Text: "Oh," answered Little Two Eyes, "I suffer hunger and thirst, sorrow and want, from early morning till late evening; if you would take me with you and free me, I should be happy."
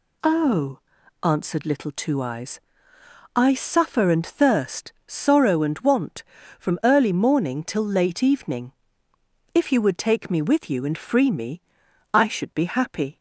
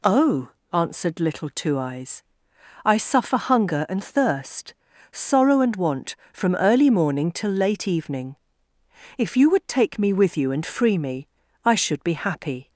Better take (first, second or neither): second